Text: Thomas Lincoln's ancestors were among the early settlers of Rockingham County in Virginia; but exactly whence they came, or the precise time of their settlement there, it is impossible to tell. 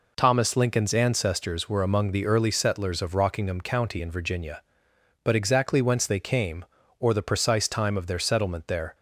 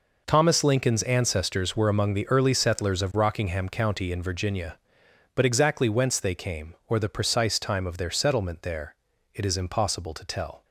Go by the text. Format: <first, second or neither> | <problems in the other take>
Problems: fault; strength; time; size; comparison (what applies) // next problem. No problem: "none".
second | stops before "it is impossible to tell"; at 8.9 s